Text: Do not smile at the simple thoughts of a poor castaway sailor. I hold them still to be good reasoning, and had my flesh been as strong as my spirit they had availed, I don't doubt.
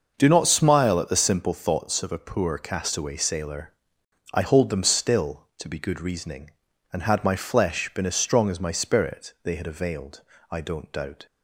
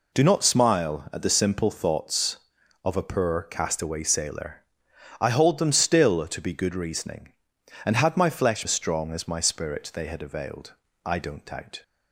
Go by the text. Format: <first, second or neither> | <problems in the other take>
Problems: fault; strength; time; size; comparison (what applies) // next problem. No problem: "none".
first | skips "been"; at 8.6 s